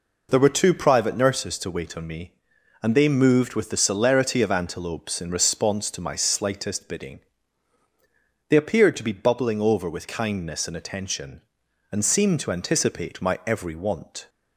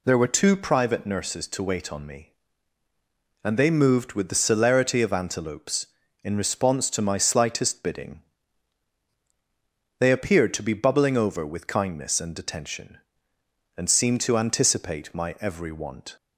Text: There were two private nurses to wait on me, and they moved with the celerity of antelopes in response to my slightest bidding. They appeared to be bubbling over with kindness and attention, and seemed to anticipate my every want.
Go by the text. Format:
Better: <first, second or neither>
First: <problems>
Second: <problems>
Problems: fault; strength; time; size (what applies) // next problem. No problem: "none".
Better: neither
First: none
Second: none